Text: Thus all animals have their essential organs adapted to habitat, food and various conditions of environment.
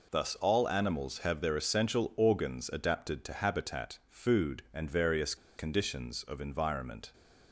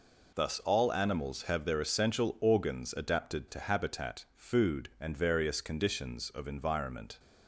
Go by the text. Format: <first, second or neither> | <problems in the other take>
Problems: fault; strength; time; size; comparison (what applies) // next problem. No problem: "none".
second | pauses between "various" and "conditions"; slight; at 5.3 s; 0.22 s long